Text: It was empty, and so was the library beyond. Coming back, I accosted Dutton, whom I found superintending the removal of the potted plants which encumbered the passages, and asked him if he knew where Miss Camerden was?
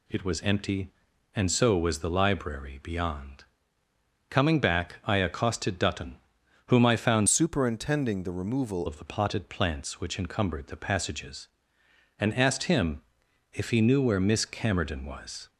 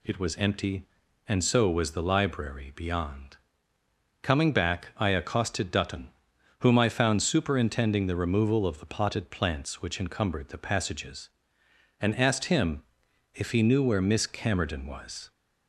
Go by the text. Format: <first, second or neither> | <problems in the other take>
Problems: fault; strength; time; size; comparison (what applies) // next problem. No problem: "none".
second | changes voice from "superintending" to "removal"; from 7.2 to 8.8 s; 1.6 s long // pauses between "him" and "if"; noticeable; at 13.0 s; 0.52 s long; noticeable in the second